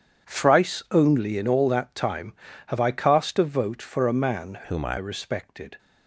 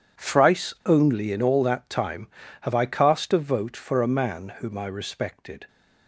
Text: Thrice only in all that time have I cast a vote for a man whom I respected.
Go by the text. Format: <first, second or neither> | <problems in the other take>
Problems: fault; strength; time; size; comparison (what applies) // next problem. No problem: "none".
second | changes voice from "whom" to "I"; from 4.6 to 4.9 s; 0.3 s long